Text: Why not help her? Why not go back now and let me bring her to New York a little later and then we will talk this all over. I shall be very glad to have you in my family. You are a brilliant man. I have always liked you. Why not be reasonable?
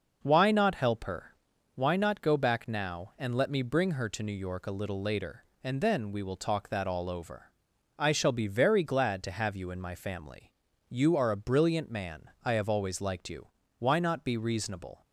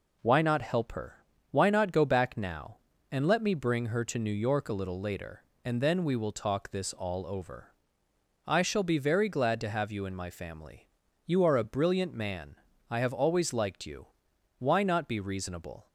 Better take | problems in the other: second | says "that" for "this"; at 6.6 s

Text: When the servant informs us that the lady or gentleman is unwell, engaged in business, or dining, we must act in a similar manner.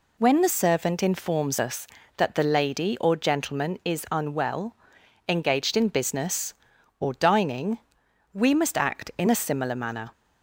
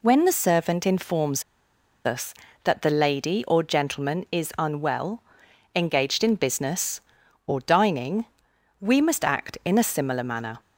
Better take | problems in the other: first | pauses between "informs" and "us"; noticeable; at 1.4 s; 0.64 s long

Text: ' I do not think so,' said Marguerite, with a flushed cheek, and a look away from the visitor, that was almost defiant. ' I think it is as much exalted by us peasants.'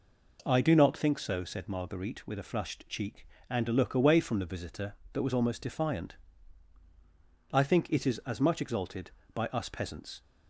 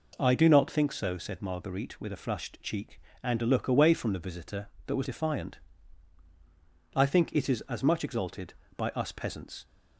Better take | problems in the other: first | skips "almost"; at 5.0 s

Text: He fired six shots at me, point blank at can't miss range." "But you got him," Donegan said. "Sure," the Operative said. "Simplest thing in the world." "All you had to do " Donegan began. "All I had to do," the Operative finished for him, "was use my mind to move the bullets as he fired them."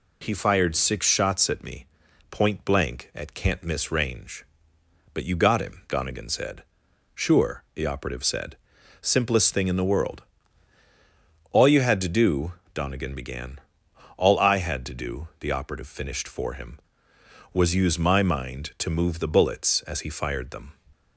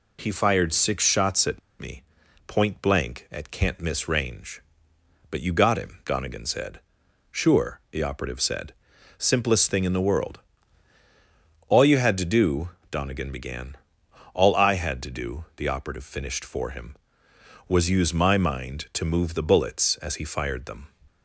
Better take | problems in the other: first | pauses between "at" and "me"; slight; at 1.6 s; 0.20 s long

